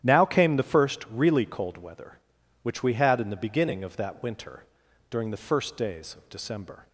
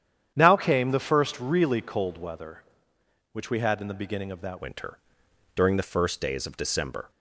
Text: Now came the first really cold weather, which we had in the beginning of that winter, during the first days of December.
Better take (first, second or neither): first